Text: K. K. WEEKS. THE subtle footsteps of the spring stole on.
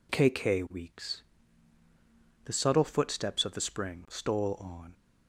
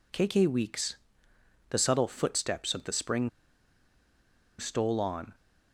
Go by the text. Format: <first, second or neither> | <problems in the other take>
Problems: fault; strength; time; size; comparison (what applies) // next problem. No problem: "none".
first | pauses between "spring" and "stole"; strong; at 3.2 s; 1.2 s long